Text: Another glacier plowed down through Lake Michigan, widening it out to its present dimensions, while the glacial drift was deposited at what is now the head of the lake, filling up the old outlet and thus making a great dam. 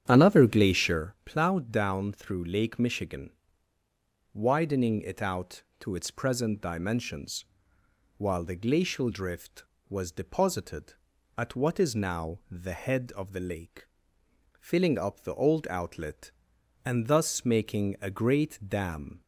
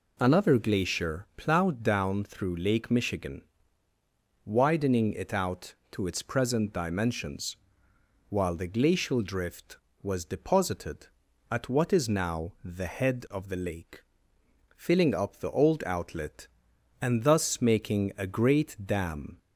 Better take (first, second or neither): second